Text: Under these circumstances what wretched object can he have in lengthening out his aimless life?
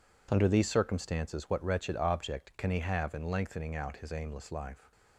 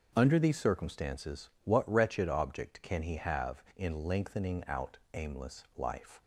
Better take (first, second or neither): first